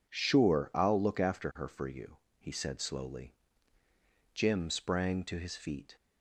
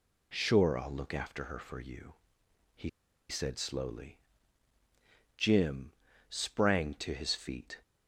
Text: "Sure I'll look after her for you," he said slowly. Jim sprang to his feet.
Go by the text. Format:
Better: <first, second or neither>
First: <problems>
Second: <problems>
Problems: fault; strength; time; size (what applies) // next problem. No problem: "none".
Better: first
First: none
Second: pauses between "he" and "said"; at 2.8 s; 0.41 s long // pauses between "Jim" and "sprang"; at 5.9 s; 0.38 s long